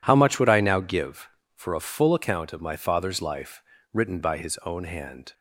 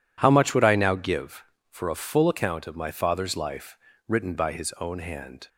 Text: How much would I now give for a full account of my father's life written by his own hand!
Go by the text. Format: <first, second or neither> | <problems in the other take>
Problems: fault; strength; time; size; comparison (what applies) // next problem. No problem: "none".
neither | pauses between "life" and "written"; slight; the same in both